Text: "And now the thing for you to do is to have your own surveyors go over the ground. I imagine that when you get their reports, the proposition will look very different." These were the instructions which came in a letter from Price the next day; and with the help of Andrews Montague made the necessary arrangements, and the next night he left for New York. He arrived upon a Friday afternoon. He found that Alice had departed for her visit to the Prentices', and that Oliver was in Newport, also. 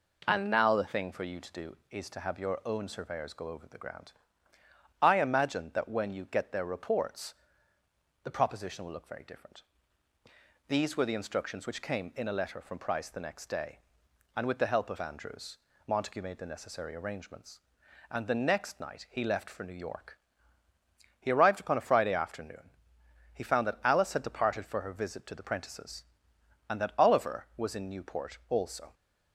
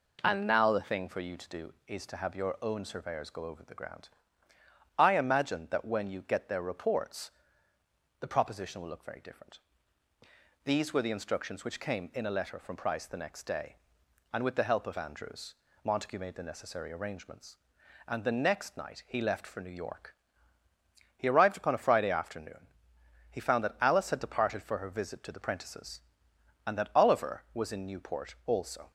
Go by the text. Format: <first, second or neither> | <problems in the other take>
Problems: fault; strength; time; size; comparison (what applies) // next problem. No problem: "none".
neither | pauses between "Andrews" and "Montague"; slight; the same in both